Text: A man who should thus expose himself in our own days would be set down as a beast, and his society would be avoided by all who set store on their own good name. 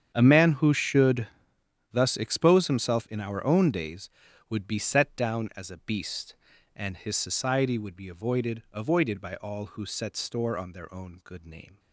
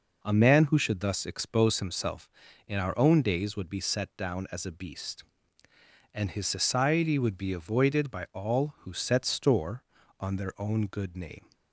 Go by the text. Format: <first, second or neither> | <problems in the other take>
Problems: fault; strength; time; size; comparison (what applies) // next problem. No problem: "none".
second | starts louder than the rest; strong; until 1.1 s; 8 dB // pauses between "should" and "thus"; noticeable; at 1.2 s; 0.66 s long // says "avoided" twice; at 8.7 s